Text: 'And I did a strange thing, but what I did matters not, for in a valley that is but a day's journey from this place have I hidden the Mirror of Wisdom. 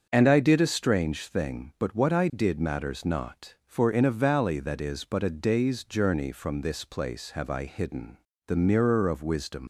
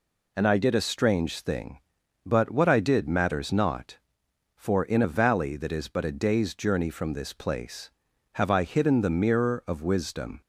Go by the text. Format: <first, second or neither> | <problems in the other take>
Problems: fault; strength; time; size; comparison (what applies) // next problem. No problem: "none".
second | starts louder than the rest; strong; until 1.1 s; 7 dB // pauses between "hidden" and "the"; slight; at 8.1 s; 0.32 s long // leaves "Wisdom" unfinished; at 9.6 s; 130 ms